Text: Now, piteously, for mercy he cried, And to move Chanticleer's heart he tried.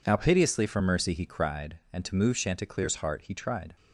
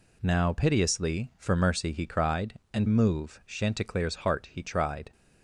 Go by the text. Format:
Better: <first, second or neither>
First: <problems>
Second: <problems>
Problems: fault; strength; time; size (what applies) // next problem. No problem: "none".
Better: first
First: none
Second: skips "to"; at 2.8 s